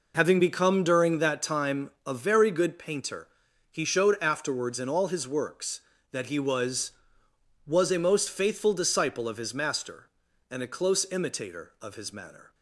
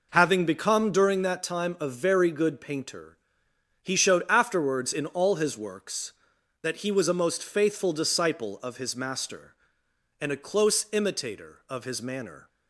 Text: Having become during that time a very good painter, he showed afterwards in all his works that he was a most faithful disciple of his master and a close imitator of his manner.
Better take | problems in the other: second | pauses between "time" and "a"; slight; at 1.8 s; 0.16 s long // says "was" twice; at 7.6 s

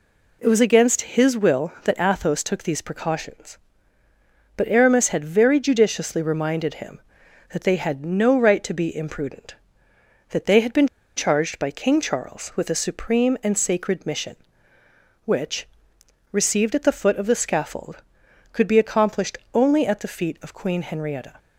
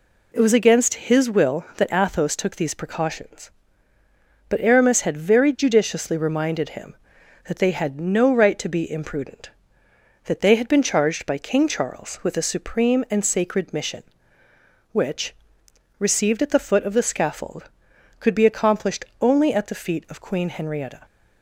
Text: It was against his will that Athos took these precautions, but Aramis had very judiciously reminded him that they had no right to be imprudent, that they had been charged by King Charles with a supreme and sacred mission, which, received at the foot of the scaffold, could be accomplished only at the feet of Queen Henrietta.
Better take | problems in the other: second | pauses between "been" and "charged"; slight; at 10.8 s; 0.28 s long // pauses between "accomplished" and "only"; slight; at 19.3 s; 0.16 s long; slight in the second

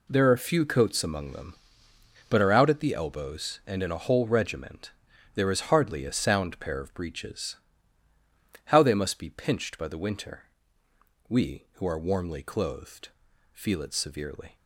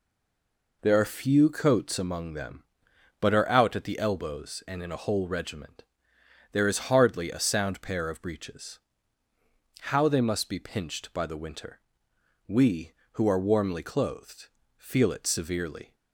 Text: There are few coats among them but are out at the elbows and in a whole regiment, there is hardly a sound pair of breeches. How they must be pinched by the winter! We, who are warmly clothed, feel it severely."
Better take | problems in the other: first | stays silent before the first word; slight; until 0.8 s; 0.8 s long

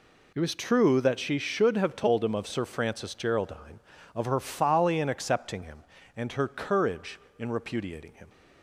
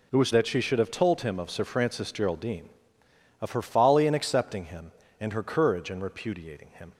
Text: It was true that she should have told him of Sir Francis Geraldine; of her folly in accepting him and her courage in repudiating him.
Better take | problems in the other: first | skips "true"; at 0.3 s

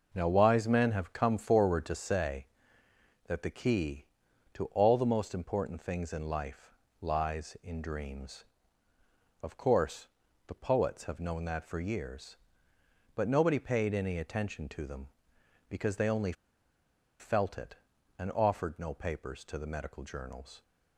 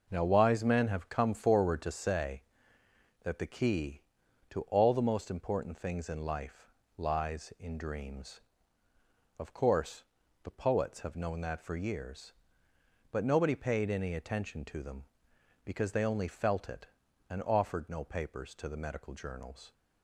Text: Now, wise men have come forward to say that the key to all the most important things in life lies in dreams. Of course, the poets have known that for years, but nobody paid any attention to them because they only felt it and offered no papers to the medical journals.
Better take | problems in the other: second | pauses between "life" and "lies"; slight; at 6.7 s; 0.26 s long; slight in the second // pauses between "only" and "felt"; noticeable; at 16.3 s; 0.86 s long

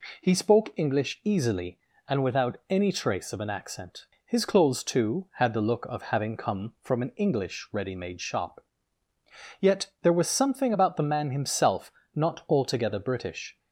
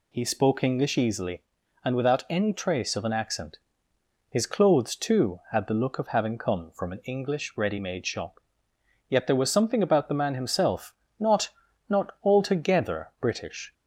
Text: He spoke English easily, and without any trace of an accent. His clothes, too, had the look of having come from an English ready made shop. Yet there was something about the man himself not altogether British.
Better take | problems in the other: first | pauses between "himself" and "not"; slight; at 10.9 s; 0.24 s long; slight in the first // says "not" twice; at 11.8 s

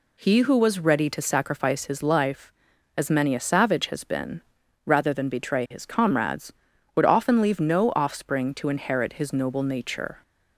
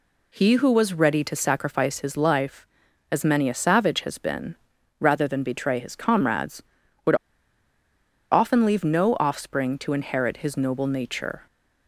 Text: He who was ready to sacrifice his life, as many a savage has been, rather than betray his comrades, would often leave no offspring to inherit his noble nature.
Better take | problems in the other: first | pauses between "would" and "often"; at 7.1 s; 1.1 s long

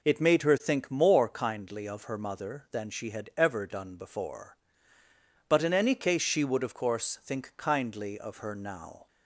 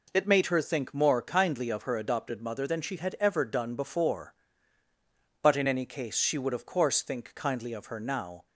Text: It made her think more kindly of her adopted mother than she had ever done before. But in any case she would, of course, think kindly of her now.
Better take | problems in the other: second | skips "adopted"; at 2.1 s

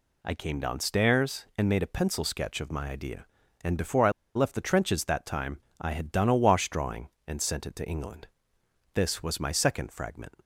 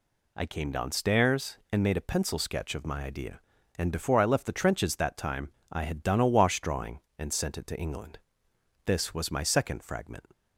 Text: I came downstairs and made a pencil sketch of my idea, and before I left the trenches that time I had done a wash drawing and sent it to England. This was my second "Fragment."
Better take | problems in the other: second | pauses between "I" and "left"; slight; at 4.1 s; 0.23 s long // pauses between "time" and "I"; slight; at 5.6 s; 0.20 s long; slight in the second

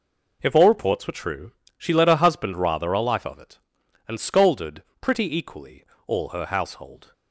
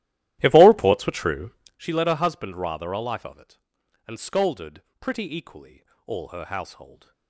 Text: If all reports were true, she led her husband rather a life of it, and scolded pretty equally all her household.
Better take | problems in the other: first | starts louder than the rest; strong; until 1.8 s; 14 dB // pauses between "scolded" and "pretty"; slight; at 4.8 s; 0.20 s long; slight in the first // pauses between "equally" and "all"; slight; at 5.8 s; 0.22 s long; slight in the first

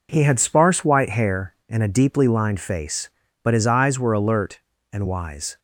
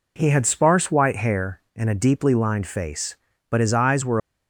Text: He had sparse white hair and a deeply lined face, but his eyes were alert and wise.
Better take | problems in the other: first | stops before "alert and wise"; at 4.1 s

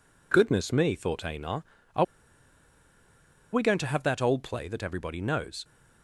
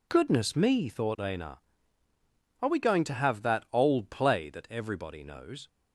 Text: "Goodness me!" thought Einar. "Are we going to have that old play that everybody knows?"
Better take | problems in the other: second | pauses between "Are" and "we"; strong; at 2.0 s; 1.4 s long

